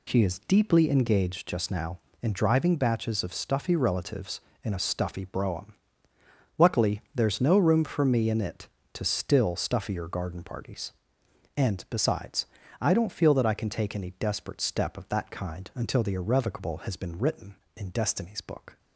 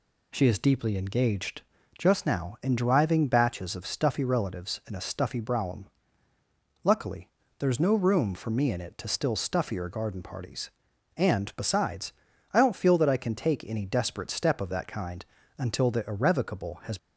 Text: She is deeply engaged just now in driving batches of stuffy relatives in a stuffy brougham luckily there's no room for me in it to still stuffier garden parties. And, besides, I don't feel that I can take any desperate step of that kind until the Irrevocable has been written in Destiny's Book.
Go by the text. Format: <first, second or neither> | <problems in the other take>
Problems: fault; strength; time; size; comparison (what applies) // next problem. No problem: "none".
first | pauses between "engaged" and "just"; slight; at 1.6 s; 0.36 s long // pauses between "brougham" and "luckily"; noticeable; at 5.8 s; 0.96 s long; noticeable in the first // pauses between "luckily" and "there's"; slight; at 7.2 s; 0.30 s long // pauses between "kind" and "until"; slight; at 15.2 s; 0.32 s long // stops before "been written in Destiny's Book"; at 16.9 s